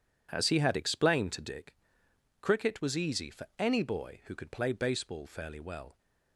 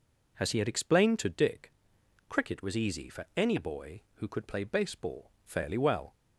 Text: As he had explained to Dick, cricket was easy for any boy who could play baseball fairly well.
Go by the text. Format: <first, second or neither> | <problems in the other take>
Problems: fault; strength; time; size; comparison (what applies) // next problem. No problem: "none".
neither | none